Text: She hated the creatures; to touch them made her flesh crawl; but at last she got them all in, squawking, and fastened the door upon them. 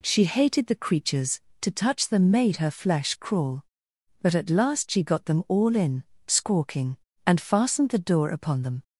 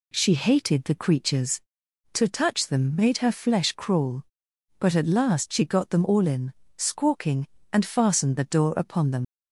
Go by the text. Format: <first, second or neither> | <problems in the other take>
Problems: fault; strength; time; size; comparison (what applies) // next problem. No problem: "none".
first | leaves "them" unfinished; at 9.2 s; 95 ms